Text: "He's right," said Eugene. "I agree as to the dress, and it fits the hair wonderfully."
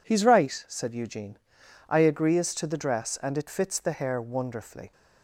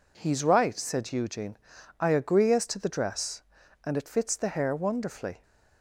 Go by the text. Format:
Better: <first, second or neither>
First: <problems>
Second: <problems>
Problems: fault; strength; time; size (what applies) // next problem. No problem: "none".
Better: neither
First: none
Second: none